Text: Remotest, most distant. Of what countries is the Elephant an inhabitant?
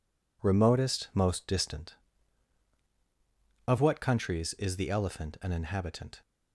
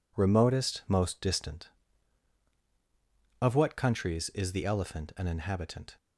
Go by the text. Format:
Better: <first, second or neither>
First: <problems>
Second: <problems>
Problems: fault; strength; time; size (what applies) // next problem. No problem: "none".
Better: neither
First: none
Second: none